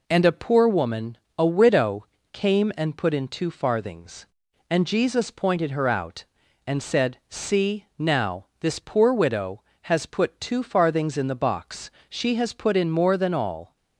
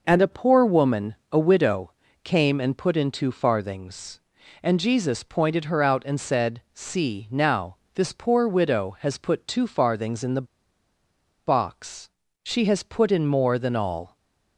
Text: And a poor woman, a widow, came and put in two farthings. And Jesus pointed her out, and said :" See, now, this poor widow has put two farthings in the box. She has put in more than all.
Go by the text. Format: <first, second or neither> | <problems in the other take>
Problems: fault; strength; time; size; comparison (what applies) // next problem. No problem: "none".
first | pauses between "the" and "box"; at 10.4 s; 0.99 s long